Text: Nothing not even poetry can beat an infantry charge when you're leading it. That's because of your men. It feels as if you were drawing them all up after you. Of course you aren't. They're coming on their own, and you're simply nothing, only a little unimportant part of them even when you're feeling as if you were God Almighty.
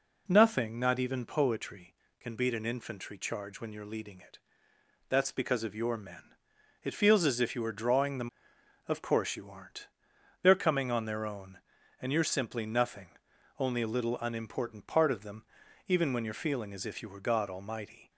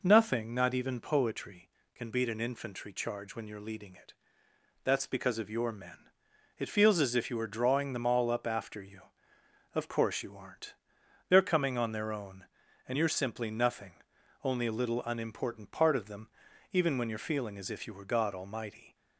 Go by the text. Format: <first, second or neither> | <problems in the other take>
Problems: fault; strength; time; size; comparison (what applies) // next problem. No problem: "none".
second | skips "all up after you"; at 8.5 s // pauses between "them" and "even"; at 15.4 s; 0.42 s long; also in the second